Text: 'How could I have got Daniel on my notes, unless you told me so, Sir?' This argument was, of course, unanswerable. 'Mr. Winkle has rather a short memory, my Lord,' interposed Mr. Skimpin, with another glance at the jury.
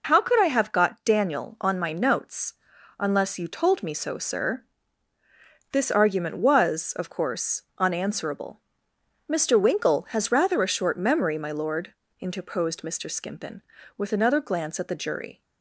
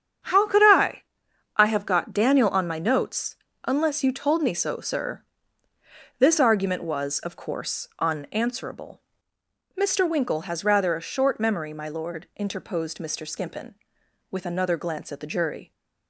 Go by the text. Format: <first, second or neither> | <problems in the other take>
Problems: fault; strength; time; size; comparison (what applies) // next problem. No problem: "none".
first | starts louder than the rest; strong; until 1.8 s; 8 dB // says "I" twice; at 1.5 s